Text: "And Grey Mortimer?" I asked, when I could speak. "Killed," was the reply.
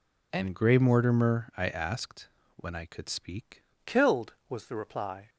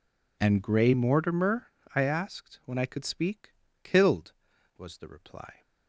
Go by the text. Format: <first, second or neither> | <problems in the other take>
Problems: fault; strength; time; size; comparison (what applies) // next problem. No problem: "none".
second | changes voice at "Killed"; from 3.8 s on; 1.4 s long